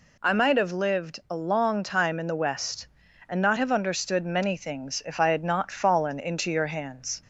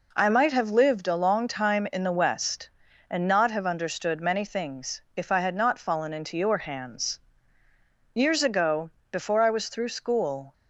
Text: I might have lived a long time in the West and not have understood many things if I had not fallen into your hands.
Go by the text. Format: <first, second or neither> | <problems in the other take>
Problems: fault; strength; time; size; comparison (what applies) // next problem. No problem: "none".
first | pauses between "things" and "if"; slight; at 4.9 s; 0.16 s long // goes on to say "Years ago before I was through school"; strong; from 8.1 s on; 2.3 s long